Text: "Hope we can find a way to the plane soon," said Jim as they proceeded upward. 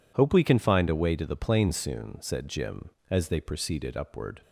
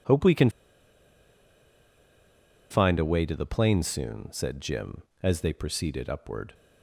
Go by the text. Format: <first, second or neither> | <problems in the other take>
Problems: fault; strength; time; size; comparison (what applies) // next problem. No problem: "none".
first | pauses between "can" and "find"; strong; at 0.4 s; 2.2 s long